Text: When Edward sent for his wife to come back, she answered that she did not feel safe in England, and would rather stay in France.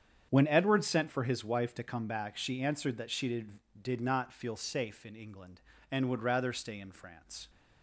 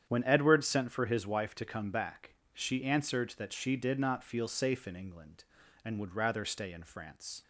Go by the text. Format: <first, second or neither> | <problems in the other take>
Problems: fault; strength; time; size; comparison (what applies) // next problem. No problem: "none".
second | starts louder than the rest; strong; until 1.3 s; 8 dB; strong in the second // says "did" twice; at 3.8 s